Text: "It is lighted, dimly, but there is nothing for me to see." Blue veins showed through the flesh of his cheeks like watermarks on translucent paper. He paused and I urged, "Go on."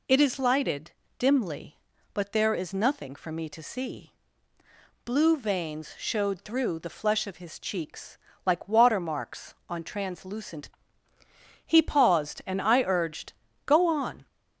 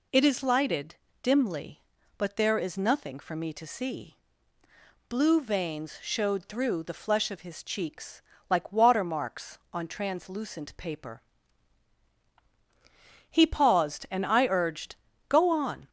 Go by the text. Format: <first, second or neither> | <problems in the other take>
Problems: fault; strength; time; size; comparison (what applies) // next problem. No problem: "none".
second | pauses between "cheeks" and "like"; slight; at 8.1 s; 0.26 s long; slight in the second // skips "paper"; at 11.1 s